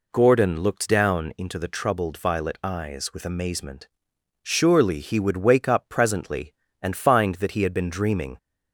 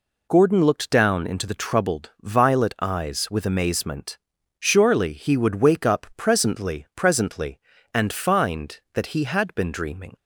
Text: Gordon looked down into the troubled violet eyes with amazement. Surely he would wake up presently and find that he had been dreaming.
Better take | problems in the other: first | says "presently" twice; at 6.9 s

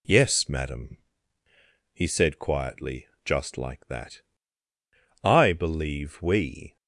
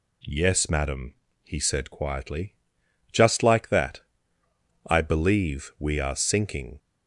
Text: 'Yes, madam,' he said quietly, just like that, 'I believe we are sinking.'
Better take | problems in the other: second | stops before "are sinking"; at 6.7 s

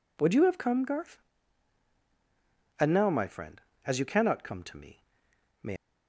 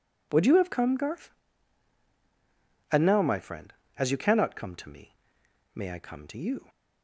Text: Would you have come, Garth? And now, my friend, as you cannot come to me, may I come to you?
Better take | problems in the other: second | stops before "I come to you"; at 5.7 s

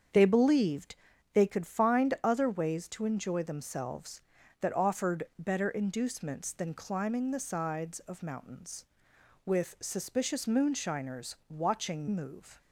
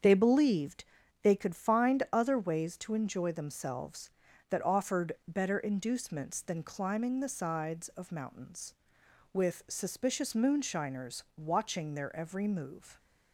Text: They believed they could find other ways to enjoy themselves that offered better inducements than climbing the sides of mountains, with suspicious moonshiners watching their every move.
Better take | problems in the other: second | starts louder than the rest; strong; until 1.5 s; 7.5 dB; strong in the second // pauses between "believed" and "they"; at 0.9 s; 0.38 s long; also in the second // skips "their every"; at 12.0 s

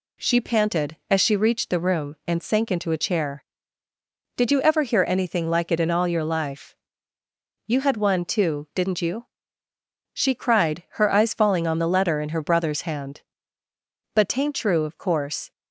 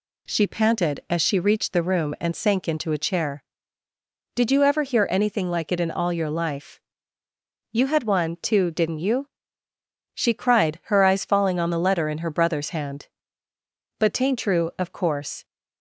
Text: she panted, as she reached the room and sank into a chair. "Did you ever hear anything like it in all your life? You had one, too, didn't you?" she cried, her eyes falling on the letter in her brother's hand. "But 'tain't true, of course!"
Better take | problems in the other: neither | none

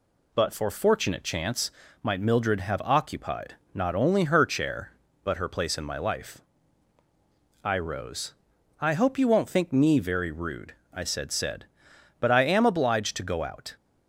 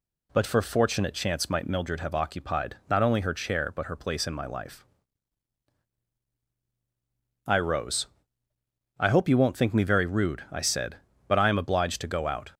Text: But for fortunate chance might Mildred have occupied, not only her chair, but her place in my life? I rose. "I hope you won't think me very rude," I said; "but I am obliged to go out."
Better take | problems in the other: second | pauses between "chance" and "might"; slight; at 1.7 s; 0.32 s long // says "said" twice; at 11.3 s

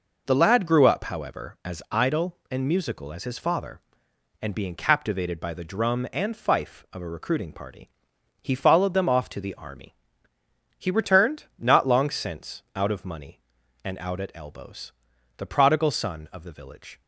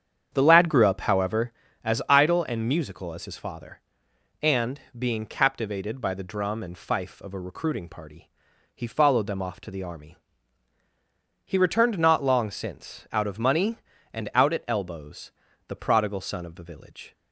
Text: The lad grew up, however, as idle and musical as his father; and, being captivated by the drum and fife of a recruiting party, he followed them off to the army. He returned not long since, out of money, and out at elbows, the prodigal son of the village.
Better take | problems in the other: first | starts louder than the rest; strong; until 1.6 s; 8 dB

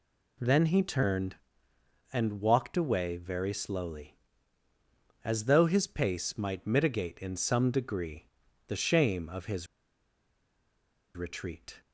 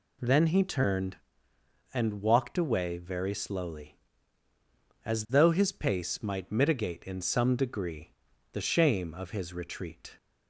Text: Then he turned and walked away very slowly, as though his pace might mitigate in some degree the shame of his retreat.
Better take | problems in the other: second | pauses between "degree" and "the"; at 8.2 s; 0.38 s long; also in the second // pauses between "his" and "retreat"; strong; at 9.6 s; 1.4 s long

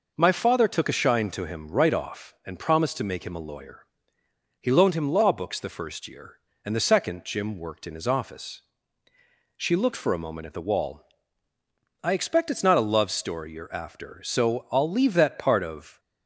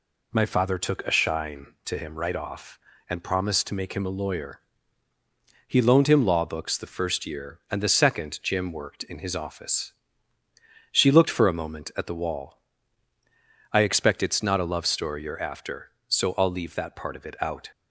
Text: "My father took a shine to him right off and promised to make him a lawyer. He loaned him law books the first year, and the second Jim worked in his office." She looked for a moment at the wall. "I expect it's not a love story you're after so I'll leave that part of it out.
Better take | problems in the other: second | stops before "it out"; at 15.9 s

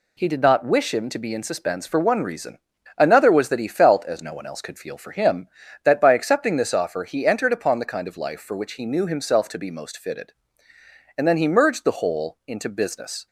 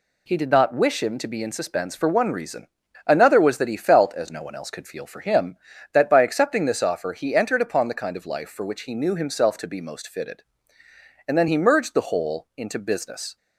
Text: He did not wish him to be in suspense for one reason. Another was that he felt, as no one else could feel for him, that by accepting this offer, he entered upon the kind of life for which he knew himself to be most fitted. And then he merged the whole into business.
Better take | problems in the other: neither | none

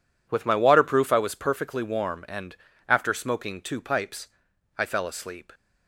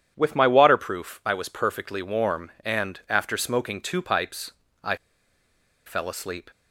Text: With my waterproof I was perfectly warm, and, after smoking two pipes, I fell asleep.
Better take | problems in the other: first | pauses between "I" and "fell"; noticeable; at 4.9 s; 0.89 s long

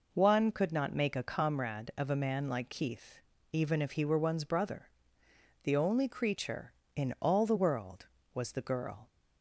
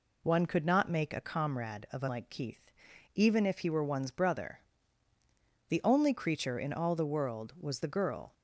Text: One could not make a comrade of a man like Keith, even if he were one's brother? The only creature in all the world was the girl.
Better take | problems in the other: first | skips "man"; at 2.0 s

